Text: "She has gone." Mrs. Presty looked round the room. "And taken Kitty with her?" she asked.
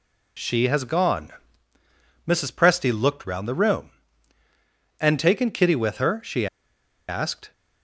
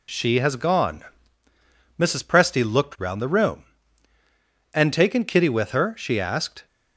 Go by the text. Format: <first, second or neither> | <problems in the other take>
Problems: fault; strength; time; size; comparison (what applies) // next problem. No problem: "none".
second | pauses between "she" and "asked"; noticeable; at 6.4 s; 0.63 s long